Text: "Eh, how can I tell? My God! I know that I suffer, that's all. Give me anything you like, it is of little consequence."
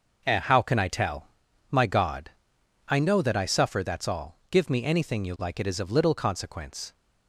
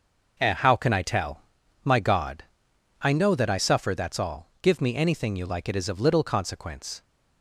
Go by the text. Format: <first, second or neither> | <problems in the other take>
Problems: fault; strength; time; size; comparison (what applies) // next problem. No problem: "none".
neither | none